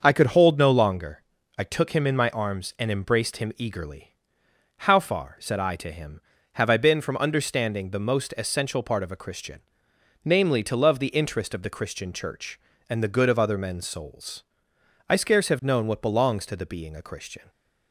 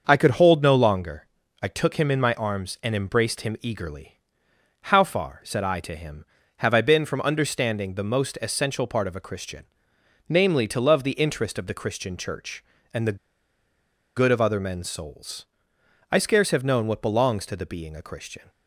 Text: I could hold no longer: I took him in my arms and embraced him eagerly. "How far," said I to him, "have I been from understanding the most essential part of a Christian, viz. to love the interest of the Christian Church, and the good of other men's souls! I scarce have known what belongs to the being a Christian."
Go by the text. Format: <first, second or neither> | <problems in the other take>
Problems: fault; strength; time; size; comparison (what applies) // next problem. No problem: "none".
first | starts louder than the rest; until 1.0 s; 6.5 dB; also in the first // pauses between "the" and "good"; at 13.1 s; 0.99 s long